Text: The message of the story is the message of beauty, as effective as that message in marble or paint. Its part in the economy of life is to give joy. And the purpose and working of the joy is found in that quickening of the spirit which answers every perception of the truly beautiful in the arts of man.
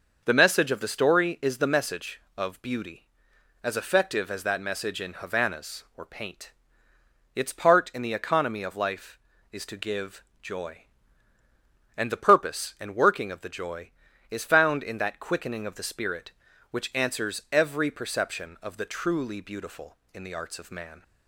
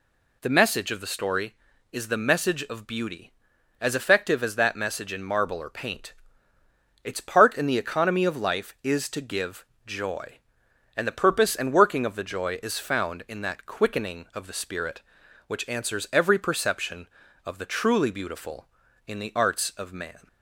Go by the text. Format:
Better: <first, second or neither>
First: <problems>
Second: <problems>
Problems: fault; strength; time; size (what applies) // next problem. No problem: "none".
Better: second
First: starts louder than the rest; until 1.2 s; 6 dB // says "havanas" for "marble"; at 5.1 s // pauses between "give" and "joy"; slight; at 10.2 s; 0.18 s long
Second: pauses between "give" and "joy"; slight; at 9.6 s; 0.22 s long